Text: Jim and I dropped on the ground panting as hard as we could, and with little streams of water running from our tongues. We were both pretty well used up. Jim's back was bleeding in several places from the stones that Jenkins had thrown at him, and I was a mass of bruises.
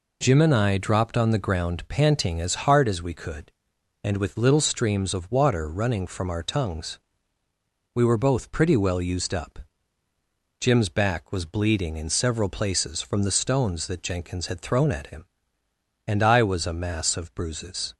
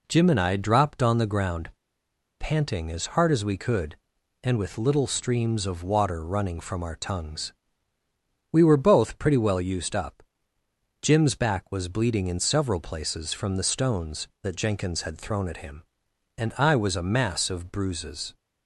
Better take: first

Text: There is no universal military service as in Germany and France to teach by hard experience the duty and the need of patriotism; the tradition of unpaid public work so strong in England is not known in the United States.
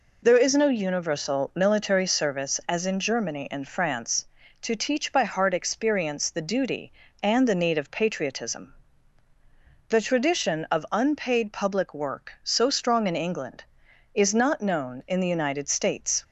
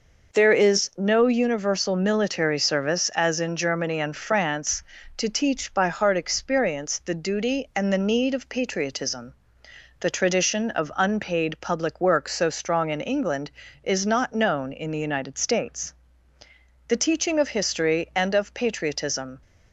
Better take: first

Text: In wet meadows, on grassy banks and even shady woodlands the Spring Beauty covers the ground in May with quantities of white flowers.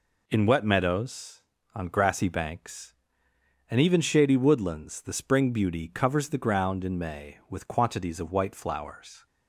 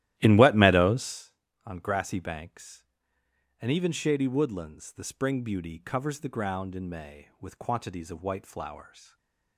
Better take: first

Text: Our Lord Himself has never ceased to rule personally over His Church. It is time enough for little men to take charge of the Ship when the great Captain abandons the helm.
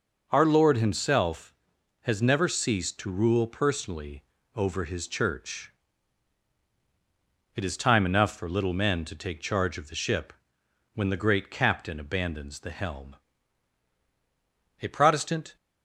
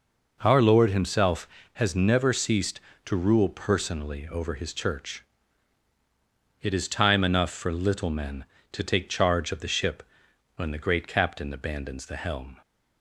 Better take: second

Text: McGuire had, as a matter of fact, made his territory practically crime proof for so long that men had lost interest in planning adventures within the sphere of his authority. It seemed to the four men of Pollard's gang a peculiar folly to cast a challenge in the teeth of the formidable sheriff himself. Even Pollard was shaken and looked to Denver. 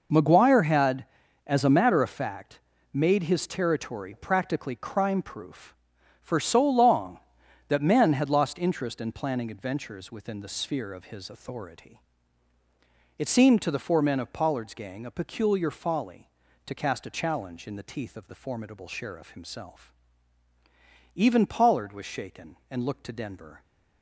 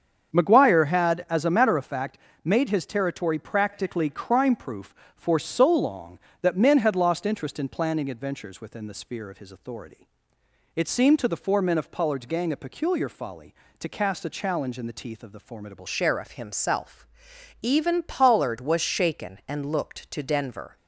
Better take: first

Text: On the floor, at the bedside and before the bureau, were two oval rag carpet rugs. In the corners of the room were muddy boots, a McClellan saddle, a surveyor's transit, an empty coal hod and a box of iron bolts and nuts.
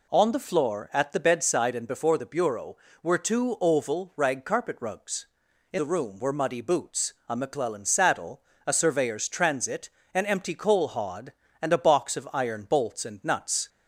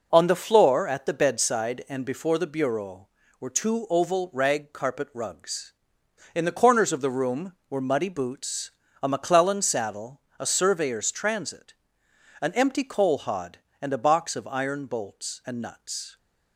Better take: second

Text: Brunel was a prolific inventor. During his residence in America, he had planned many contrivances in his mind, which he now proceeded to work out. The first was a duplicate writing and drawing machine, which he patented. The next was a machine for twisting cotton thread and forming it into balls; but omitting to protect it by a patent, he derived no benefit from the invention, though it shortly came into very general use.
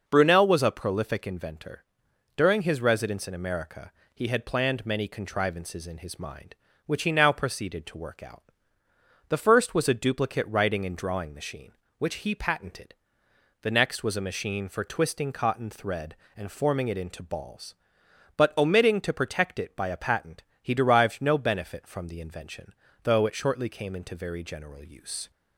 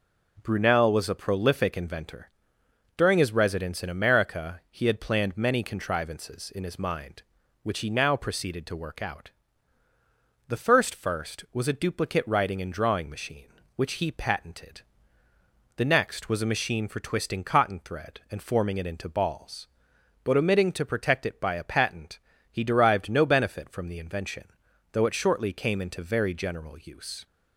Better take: first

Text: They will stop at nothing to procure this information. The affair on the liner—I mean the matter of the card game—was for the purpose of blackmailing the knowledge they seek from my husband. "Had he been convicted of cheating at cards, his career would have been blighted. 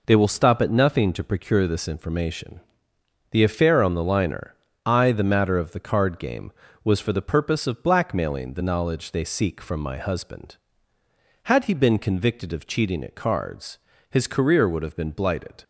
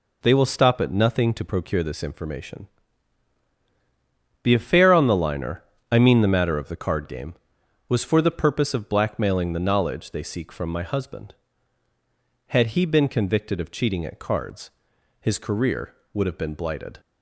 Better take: second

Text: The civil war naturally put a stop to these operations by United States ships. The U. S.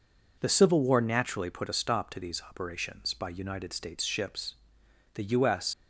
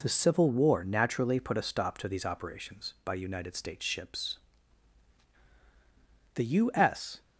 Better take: second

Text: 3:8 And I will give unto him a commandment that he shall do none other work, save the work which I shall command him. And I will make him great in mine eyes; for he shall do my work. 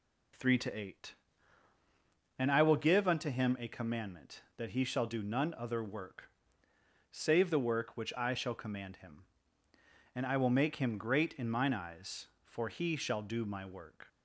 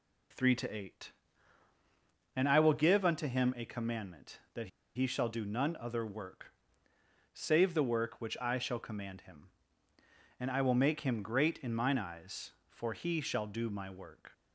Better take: first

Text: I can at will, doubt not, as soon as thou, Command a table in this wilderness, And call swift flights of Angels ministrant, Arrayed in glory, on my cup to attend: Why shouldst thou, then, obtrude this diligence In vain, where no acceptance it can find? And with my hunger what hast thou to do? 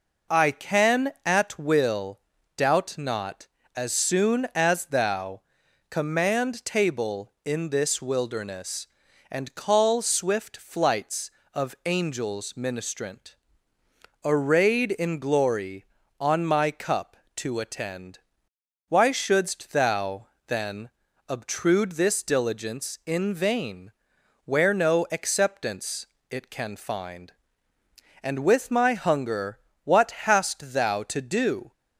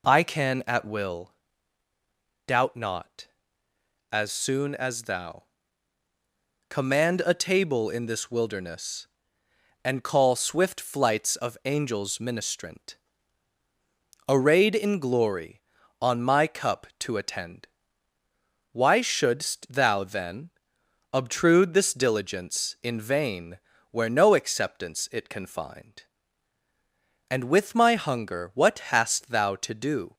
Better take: second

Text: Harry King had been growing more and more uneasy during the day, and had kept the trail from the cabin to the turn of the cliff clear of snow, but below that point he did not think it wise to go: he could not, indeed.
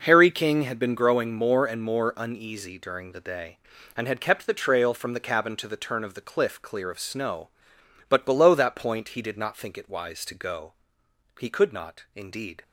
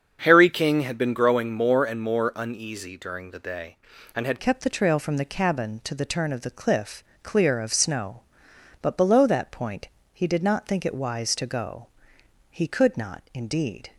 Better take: first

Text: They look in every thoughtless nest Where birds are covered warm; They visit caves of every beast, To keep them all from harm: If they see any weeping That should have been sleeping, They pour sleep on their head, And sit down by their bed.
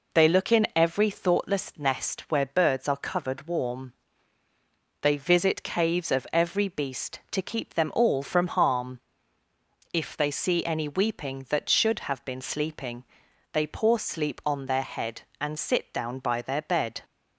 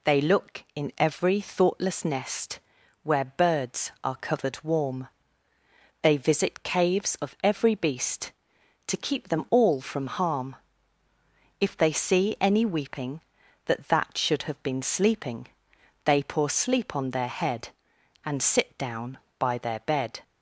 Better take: first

